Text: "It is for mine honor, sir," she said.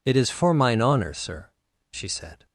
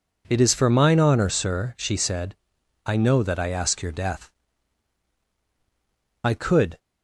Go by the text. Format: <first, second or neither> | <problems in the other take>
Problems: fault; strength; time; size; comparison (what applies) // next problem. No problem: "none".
first | goes on to say "I know that I ask your death I could"; strong; from 2.8 s on; 3.9 s long